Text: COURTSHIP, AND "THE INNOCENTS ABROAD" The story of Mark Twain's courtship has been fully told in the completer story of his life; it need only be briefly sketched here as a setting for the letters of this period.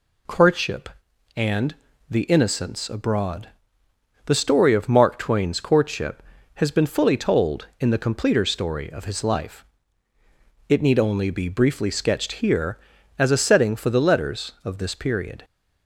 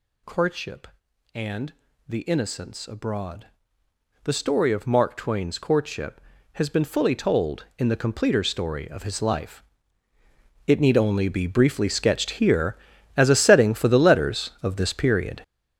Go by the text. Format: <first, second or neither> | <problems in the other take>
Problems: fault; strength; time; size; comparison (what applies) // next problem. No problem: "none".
first | gets louder; strong; throughout; 10 dB // pauses between "AND" and "THE"; slight; at 1.7 s; 0.34 s long; slight in the first // pauses between "ABROAD" and "The"; noticeable; at 3.4 s; 0.76 s long; noticeable in the first